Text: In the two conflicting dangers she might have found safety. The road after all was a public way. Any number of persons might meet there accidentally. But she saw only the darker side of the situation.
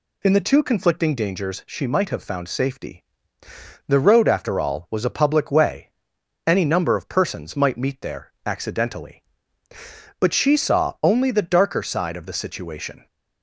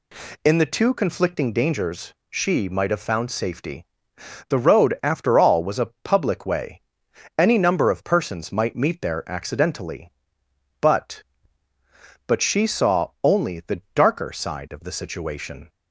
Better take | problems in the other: first | pauses between "dangers" and "she"; slight; at 2.1 s; 0.16 s long // says "But" twice; at 12.2 s

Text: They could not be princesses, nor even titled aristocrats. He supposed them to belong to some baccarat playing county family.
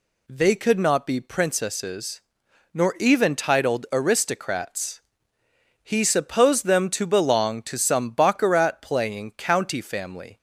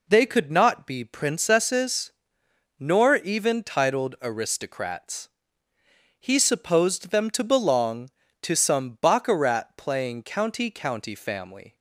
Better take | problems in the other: first | says "county" twice; at 10.6 s

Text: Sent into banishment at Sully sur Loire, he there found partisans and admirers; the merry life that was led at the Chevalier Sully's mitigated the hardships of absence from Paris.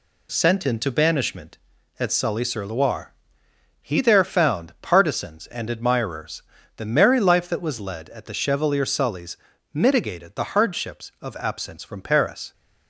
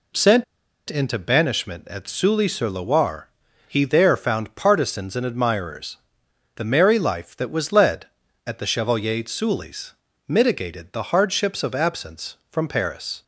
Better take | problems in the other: first | pauses between "Sent" and "into"; at 0.4 s; 0.44 s long // pauses between "Sully's" and "mitigated"; slight; at 9.9 s; 0.36 s long; also in the first

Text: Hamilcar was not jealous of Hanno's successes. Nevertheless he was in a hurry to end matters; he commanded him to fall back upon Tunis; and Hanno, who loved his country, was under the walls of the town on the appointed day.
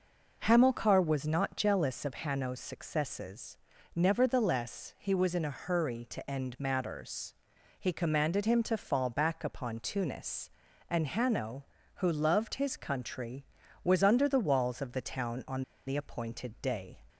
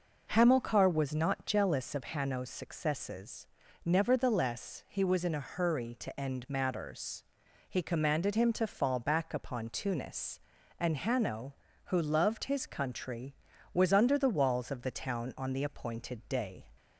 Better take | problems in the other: second | pauses between "on" and "the"; slight; at 15.6 s; 0.24 s long

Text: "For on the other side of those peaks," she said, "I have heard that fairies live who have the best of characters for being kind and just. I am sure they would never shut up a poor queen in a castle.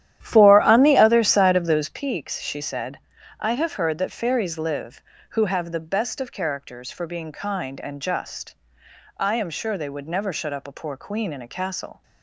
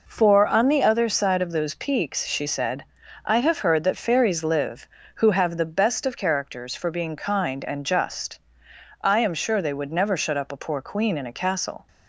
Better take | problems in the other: second | starts louder than the rest; strong; until 2.0 s; 11.5 dB

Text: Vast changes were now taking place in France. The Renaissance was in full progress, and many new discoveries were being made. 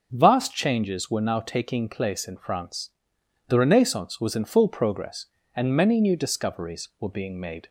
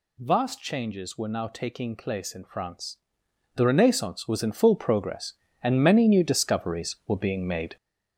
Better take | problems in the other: first | gets louder; throughout; 6.5 dB

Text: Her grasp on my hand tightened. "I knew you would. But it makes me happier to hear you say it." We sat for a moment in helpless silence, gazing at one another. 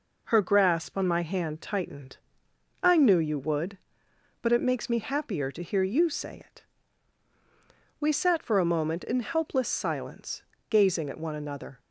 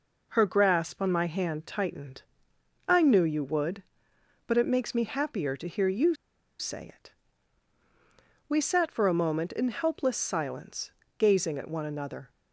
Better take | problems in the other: first | pauses between "you" and "say"; at 6.1 s; 0.45 s long

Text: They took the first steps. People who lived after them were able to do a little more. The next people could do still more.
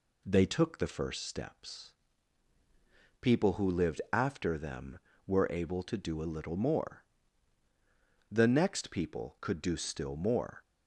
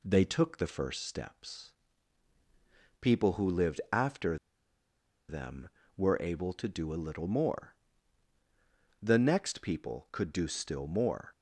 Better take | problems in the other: first | pauses between "after" and "them"; noticeable; at 4.3 s; 0.92 s long

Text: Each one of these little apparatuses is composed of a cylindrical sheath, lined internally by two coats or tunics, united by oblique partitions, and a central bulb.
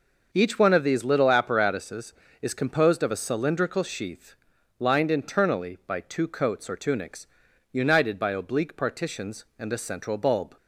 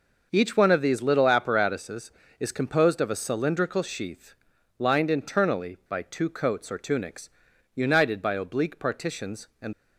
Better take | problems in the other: first | stops before "a central bulb"; at 9.7 s

